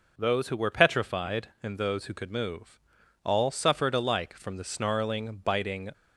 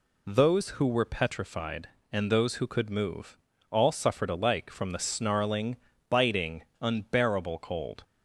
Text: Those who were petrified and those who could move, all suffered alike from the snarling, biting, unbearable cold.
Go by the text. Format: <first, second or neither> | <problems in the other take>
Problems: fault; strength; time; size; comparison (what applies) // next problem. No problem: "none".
second | stops before "unbearable cold"; at 5.9 s